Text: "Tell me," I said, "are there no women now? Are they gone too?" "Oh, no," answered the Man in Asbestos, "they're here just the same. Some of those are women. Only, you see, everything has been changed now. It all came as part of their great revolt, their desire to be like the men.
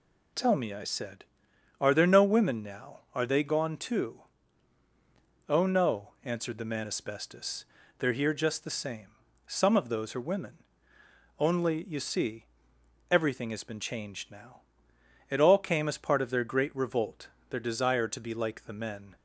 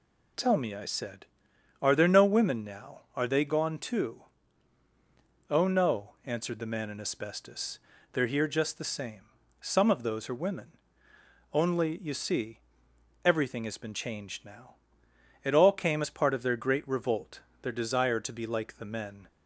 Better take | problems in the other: second | skips "in"; at 6.8 s

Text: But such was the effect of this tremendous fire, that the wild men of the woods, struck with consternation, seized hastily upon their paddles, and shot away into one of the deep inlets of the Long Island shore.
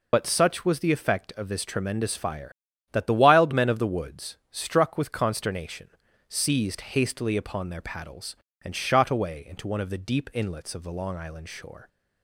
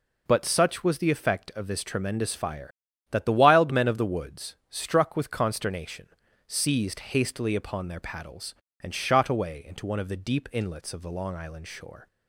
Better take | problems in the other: second | loses the start of "But"; at 0.1 s; 50 ms

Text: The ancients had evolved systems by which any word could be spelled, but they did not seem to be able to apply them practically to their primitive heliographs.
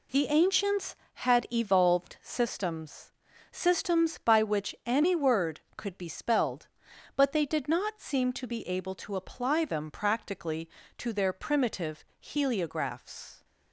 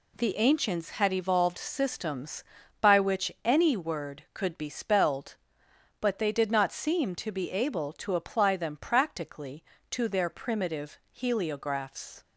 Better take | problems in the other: second | says "systems" twice; at 3.5 s // pauses between "primitive" and "heliographs"; slight; at 12.0 s; 0.16 s long

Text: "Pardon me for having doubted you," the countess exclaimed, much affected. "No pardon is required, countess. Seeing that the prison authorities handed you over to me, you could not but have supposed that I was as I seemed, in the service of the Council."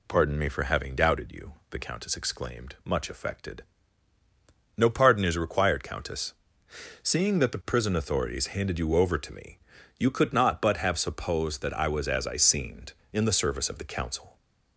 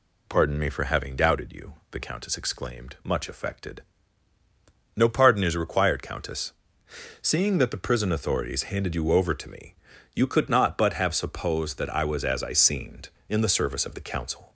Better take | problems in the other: neither | none

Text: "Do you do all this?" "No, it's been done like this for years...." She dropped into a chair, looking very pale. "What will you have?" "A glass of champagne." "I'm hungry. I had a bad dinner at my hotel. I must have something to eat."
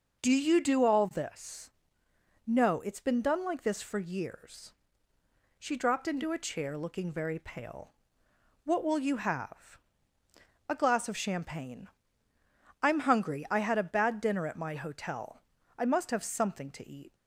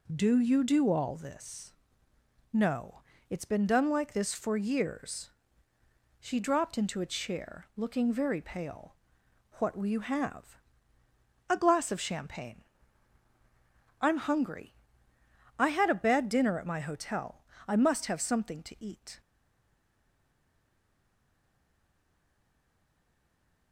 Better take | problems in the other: first | stays silent after the last word; strong; from 19.2 s on; 4.5 s long

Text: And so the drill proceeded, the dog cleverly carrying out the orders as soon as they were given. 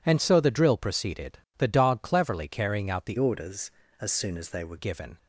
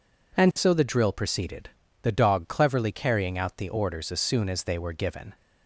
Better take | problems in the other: second | changes voice from "orders" to "were"; from 3.1 to 4.7 s; 1.6 s long

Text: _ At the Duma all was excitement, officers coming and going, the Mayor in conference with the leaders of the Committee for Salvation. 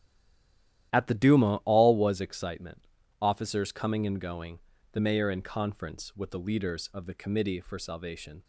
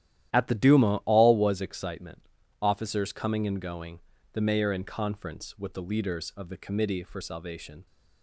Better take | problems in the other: second | stays silent before the first word; slight; until 0.9 s; 0.9 s long // starts louder than the rest; strong; until 1.9 s; 12 dB; strong in the second

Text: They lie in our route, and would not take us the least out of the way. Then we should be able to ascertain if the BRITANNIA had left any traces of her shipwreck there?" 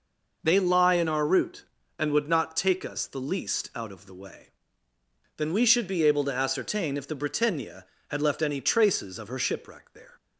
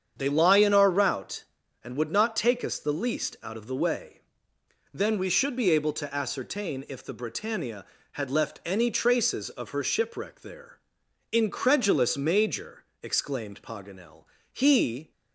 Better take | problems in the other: first | starts louder than the rest; strong; until 1.1 s; 8 dB // goes on to say "Incredulous Major exclaimed Paganel he"; strong; from 11.3 s on; 3.8 s long

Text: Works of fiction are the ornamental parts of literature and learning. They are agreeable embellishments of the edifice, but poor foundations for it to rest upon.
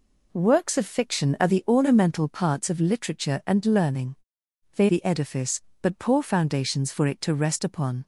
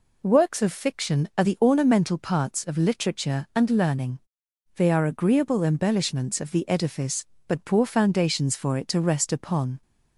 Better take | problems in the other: second | skips "are agreeable embellishments of"; at 4.8 s

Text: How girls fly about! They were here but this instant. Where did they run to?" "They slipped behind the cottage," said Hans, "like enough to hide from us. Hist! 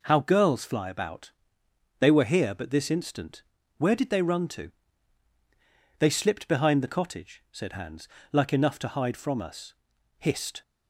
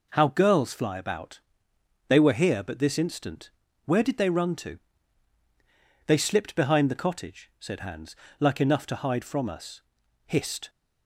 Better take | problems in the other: neither | none

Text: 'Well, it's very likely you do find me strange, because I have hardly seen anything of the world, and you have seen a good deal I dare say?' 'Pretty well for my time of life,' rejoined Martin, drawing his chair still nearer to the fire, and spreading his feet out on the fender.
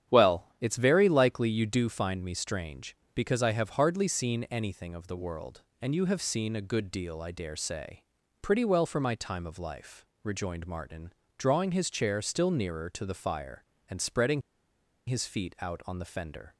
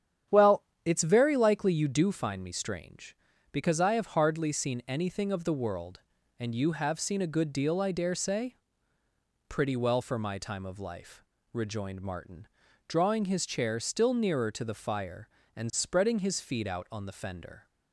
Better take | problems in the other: second | starts louder than the rest; strong; until 1.2 s; 9.5 dB; strong in the second // pauses between "spreading" and "his"; noticeable; at 14.4 s; 0.66 s long

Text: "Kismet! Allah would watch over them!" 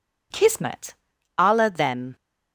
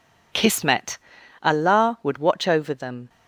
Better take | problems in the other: second | skips "would watch over"; at 1.7 s

